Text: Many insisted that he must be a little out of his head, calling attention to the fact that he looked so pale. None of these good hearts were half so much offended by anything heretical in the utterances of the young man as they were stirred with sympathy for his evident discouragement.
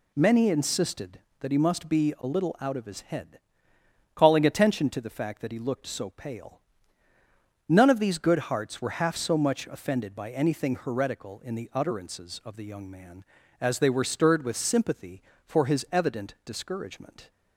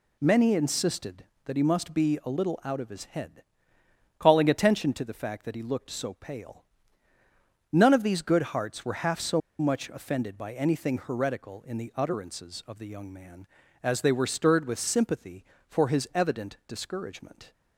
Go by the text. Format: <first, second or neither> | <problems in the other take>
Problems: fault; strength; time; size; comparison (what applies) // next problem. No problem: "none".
first | pauses between "so" and "much"; slight; at 9.4 s; 0.20 s long